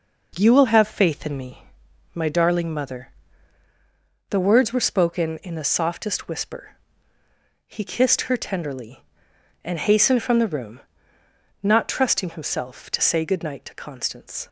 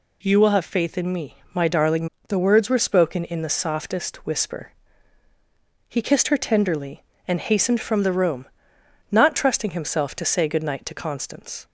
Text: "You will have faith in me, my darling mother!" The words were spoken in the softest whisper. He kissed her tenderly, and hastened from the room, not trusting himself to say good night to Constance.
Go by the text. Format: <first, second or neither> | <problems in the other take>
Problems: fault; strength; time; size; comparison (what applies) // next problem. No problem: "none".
first | skips "mother"; at 2.1 s